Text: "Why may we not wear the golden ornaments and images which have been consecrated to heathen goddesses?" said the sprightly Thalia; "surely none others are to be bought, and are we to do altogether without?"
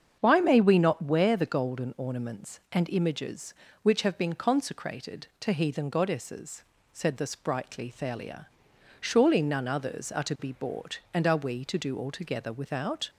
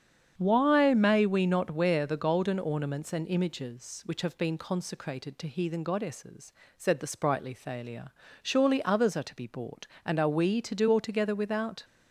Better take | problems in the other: first | starts louder than the rest; strong; until 1.3 s; 8.5 dB; strong in the first // skips "none"; at 8.8 s

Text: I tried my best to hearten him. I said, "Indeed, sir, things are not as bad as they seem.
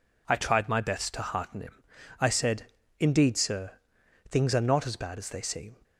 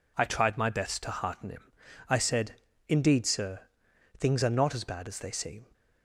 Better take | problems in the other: neither | none

